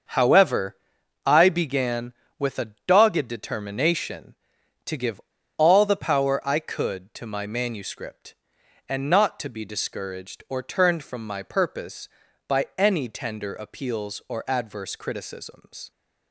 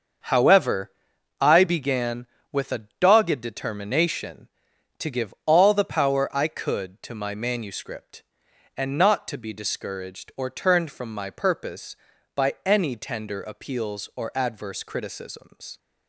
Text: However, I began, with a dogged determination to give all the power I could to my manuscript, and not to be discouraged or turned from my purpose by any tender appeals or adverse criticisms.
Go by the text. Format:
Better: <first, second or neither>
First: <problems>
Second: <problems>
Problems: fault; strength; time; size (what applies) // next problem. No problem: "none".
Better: second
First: starts louder than the rest; until 1.5 s; 6.5 dB // pauses between "give" and "all"; at 5.1 s; 0.39 s long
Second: starts louder than the rest; until 1.7 s; 6.5 dB